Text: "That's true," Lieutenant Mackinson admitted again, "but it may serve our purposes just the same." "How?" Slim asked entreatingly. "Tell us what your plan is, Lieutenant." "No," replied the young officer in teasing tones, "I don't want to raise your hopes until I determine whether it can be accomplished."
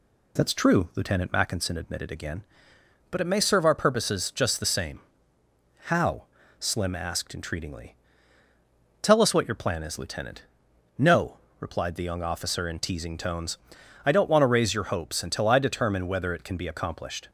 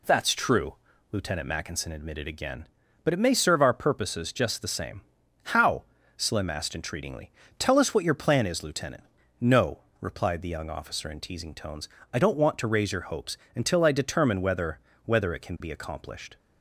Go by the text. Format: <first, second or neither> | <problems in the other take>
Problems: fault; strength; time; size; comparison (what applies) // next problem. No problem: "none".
first | pauses between "hopes" and "until"; slight; at 13.3 s; 0.18 s long // says "whether" twice; at 15.0 s